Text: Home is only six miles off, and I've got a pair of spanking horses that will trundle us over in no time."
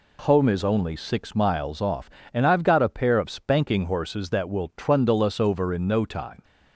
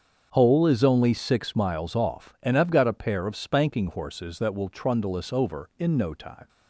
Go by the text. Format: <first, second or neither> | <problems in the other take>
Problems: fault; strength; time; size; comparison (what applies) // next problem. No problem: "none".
first | starts louder than the rest; strong; until 1.3 s; 7 dB // says "Hole" for "Home"; at 0.3 s